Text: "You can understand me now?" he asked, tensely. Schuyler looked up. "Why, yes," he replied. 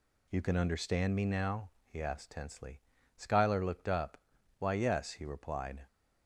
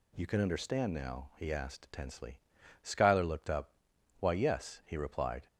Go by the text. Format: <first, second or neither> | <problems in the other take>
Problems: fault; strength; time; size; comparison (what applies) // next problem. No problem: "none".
first | skips "me"; at 0.9 s